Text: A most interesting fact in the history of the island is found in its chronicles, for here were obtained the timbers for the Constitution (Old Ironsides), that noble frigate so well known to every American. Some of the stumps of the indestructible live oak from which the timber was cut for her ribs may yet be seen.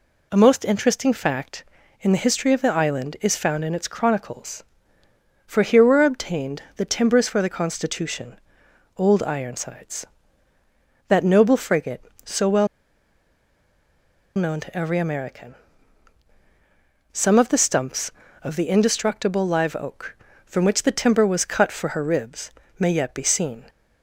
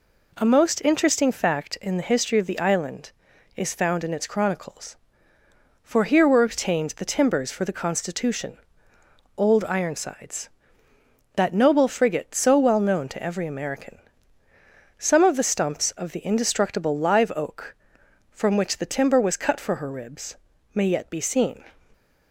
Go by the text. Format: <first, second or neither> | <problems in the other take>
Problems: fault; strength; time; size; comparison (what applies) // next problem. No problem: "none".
second | pauses between "well" and "known"; strong; at 12.6 s; 1.6 s long // pauses between "ribs" and "may"; slight; at 22.5 s; 0.26 s long; slight in the second